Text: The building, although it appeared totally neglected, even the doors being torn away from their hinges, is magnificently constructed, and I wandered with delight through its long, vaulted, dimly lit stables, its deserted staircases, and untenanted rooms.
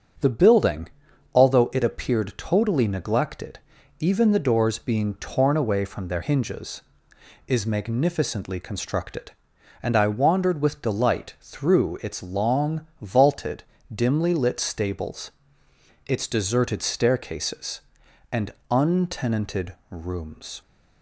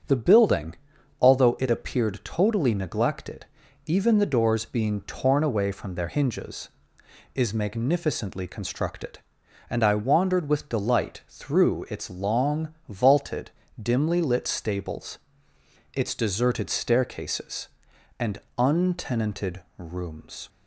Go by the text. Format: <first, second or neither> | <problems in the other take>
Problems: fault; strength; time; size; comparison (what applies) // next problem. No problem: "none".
neither | starts louder than the rest; the same in both // pauses between "and" and "untenanted"; slight; the same in both // pauses between "untenanted" and "rooms"; slight; the same in both